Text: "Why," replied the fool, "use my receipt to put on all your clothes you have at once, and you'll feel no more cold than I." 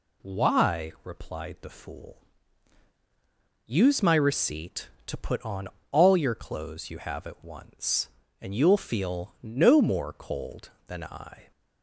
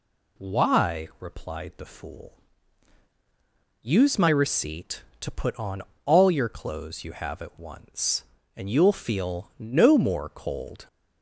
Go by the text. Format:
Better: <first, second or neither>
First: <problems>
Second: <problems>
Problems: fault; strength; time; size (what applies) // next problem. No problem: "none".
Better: first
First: pauses between "on" and "all"; slight; at 5.6 s; 0.24 s long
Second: pauses between "on" and "all"; slight; at 5.8 s; 0.24 s long // stops before "than I"; at 10.8 s